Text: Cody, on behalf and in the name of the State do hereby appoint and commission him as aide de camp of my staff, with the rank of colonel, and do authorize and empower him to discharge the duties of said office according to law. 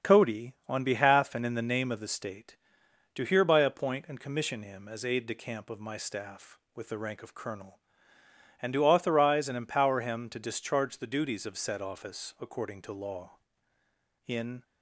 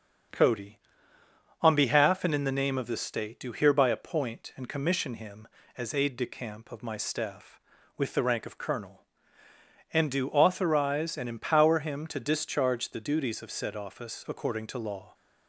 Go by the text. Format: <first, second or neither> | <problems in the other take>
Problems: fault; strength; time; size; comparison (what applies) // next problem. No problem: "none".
second | starts louder than the rest; strong; until 1.1 s; 7 dB; also in the second // goes on to say "In"; slight; from 14.2 s on; 0.36 s long